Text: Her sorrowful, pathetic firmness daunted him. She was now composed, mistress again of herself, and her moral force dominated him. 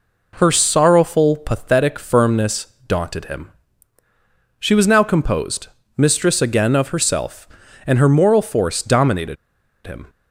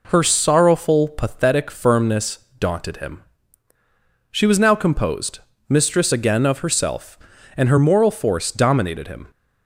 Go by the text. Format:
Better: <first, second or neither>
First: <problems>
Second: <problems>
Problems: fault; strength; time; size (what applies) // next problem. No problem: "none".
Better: second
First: pauses between "firmness" and "daunted"; slight; at 2.6 s; 0.22 s long // pauses between "dominated" and "him"; noticeable; at 9.3 s; 0.50 s long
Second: pauses between "firmness" and "daunted"; slight; at 2.3 s; 0.22 s long